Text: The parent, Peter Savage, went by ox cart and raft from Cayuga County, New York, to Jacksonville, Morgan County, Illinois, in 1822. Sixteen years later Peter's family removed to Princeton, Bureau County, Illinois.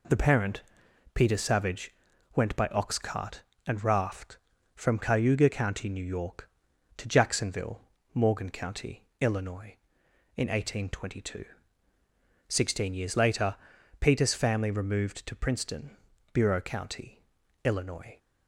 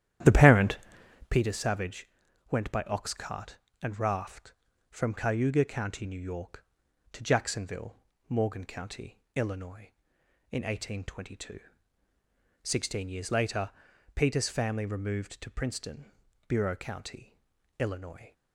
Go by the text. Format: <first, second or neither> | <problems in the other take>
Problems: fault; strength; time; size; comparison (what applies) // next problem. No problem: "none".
first | starts louder than the rest; strong; until 1.4 s; 11 dB // pauses between "later" and "Peter's"; at 13.7 s; 0.44 s long; also in the first